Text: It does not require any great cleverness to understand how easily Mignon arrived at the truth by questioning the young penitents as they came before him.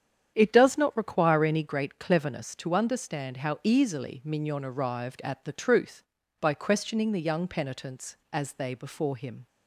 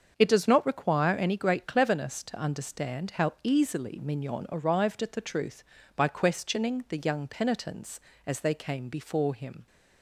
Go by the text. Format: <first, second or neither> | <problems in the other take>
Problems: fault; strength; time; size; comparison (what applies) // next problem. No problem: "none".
second | starts louder than the rest; strong; until 1.3 s; 9 dB; also in the second // skips "came"; at 8.7 s